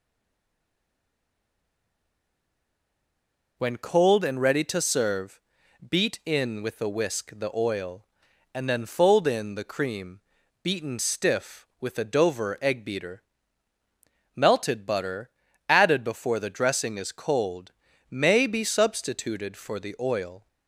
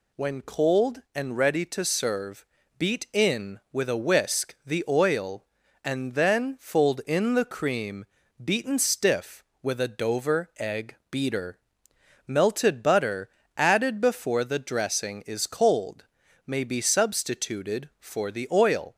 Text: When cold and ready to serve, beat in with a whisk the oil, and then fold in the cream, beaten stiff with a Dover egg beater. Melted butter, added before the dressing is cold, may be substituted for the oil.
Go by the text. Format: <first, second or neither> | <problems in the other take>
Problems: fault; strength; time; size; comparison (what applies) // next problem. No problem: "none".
second | stays silent before the first word; strong; until 3.5 s; 3.5 s long